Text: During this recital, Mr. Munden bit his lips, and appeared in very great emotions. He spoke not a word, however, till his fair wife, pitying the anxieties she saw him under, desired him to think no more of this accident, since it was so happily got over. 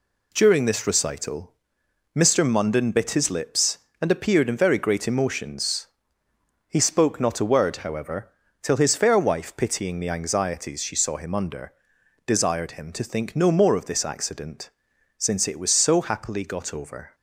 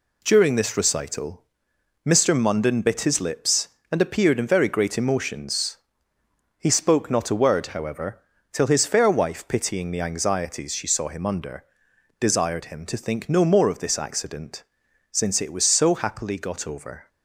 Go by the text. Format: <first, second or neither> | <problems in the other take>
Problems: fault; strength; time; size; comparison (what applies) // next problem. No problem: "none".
neither | none